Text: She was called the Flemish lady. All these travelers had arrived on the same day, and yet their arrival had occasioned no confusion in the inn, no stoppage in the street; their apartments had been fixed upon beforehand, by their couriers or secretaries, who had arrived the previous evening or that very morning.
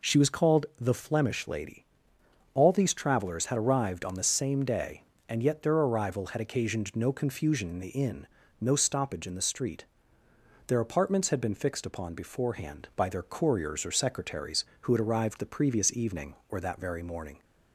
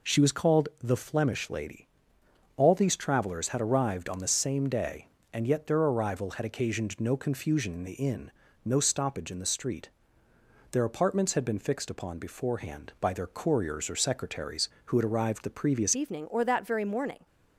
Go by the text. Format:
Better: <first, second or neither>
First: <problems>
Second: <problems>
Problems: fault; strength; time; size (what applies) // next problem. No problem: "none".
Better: first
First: none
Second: changes voice at "evening"; from 15.9 s on; 1.3 s long